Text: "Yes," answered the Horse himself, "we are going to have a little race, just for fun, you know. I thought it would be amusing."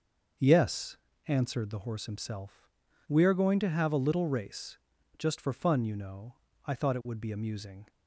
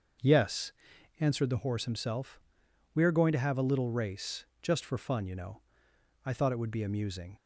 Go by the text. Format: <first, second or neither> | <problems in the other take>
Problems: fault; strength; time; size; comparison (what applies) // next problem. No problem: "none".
neither | starts louder than the rest; the same in both